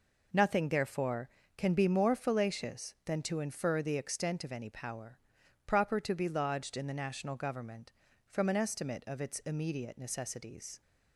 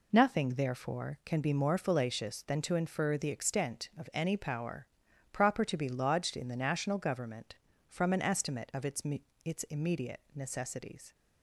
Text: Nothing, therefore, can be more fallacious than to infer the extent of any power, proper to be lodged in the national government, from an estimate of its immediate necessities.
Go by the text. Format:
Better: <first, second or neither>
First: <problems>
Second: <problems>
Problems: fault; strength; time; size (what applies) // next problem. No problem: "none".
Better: first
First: none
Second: says "its" twice; at 9.4 s